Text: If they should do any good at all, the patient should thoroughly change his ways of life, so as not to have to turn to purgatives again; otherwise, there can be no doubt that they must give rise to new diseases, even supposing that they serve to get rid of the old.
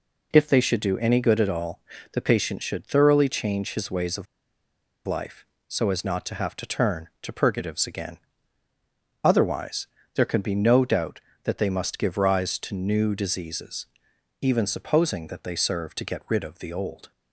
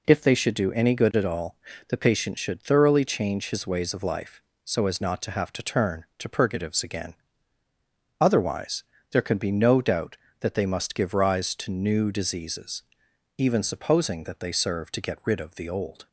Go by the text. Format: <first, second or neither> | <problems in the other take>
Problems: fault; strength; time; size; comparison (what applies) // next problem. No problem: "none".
second | pauses between "of" and "life"; noticeable; at 4.2 s; 0.81 s long